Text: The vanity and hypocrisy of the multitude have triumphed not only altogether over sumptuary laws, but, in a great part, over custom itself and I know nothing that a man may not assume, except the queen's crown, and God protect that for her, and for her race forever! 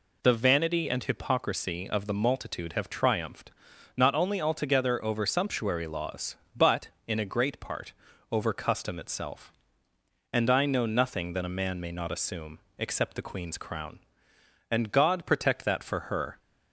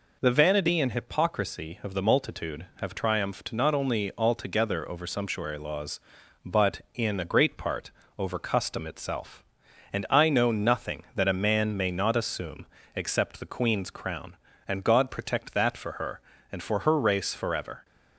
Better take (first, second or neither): second